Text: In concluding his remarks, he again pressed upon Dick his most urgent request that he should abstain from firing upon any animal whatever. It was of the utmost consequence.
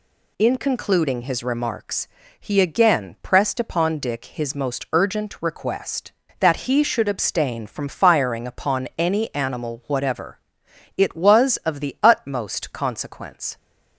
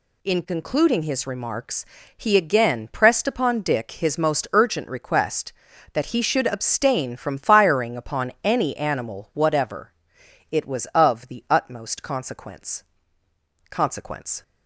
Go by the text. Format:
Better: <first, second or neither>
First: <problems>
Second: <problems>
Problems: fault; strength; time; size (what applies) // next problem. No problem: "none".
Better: first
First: none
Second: says "consequence" twice; at 13.7 s